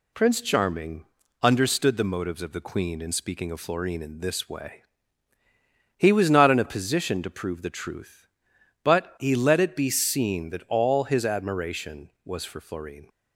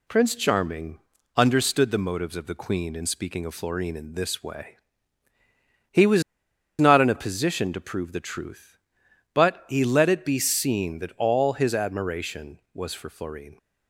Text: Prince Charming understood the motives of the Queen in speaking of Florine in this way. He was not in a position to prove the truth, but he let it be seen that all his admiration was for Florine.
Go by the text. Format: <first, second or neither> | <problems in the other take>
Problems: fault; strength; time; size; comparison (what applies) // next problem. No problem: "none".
first | pauses between "Charming" and "understood"; slight; at 0.9 s; 0.36 s long; slight in the first // pauses between "was" and "not"; noticeable; at 6.2 s; 0.56 s long